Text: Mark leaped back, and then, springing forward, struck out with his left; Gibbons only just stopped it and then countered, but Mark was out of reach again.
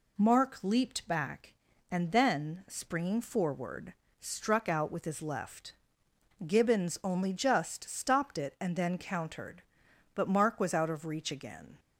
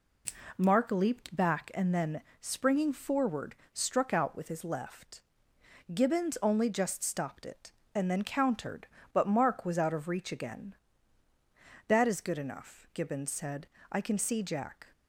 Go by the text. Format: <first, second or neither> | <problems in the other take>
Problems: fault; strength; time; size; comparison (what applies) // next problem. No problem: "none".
first | goes on to say "That is good enough Gibbons said I can see Jack"; strong; from 11.8 s on; 2.9 s long